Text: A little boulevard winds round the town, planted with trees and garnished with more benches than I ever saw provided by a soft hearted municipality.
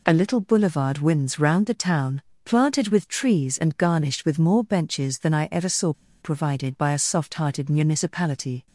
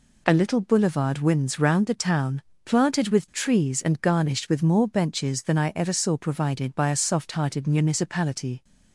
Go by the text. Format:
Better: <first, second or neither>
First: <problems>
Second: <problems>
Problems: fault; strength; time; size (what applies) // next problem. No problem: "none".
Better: second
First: pauses between "saw" and "provided"; slight; at 5.9 s; 0.29 s long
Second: none